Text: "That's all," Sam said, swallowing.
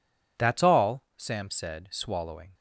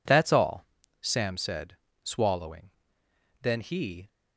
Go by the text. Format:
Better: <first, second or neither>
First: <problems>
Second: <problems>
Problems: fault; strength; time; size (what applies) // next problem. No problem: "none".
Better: first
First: none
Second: goes on to say "Then he"; noticeable; from 3.4 s on; 0.66 s long